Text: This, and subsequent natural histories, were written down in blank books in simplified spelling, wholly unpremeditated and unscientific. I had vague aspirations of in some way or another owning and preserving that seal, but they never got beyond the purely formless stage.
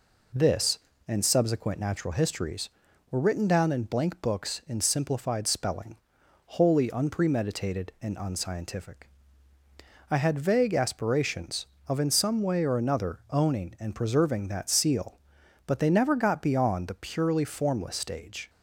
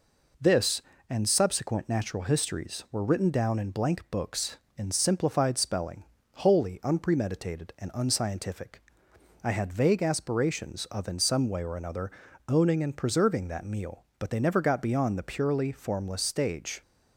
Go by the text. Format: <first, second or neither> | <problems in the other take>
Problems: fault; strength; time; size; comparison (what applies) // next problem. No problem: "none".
first | pauses between "another" and "owning"; slight; at 12.1 s; 0.36 s long // says "meal" for "seal"; at 13.6 s